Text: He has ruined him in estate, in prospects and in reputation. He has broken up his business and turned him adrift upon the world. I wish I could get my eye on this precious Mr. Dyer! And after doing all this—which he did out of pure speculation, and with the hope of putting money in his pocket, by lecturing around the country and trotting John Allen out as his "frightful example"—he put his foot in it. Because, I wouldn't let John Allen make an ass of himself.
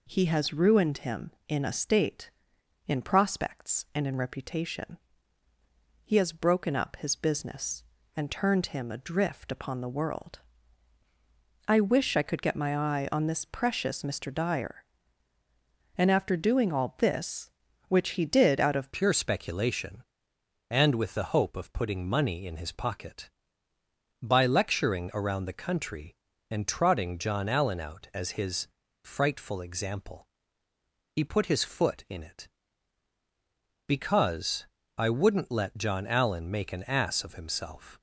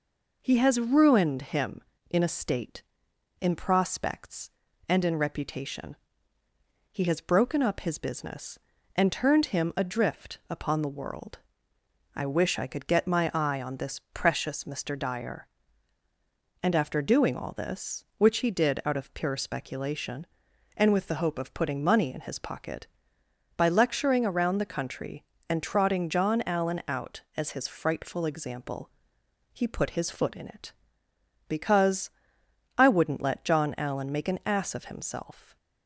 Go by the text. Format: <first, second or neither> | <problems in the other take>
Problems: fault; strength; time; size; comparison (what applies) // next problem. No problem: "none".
second | changes voice at "pure"; from 18.9 s on; 19.0 s long // pauses between "his" and "frightful"; slight; at 28.6 s; 0.36 s long